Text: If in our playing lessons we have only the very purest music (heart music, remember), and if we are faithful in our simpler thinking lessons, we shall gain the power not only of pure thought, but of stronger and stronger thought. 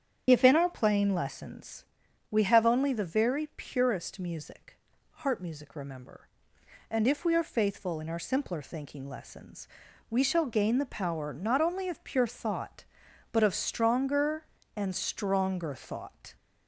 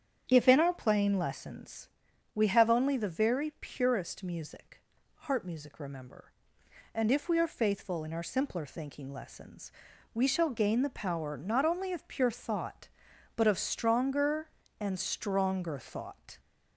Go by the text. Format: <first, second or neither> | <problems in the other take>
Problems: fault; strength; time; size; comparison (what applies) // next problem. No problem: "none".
second | loses the start of "If"; at 0.2 s; 30 ms // starts louder than the rest; strong; until 1.2 s; 9 dB; strong in the second // pauses between "lessons" and "we"; noticeable; at 1.8 s; 0.48 s long; noticeable in the second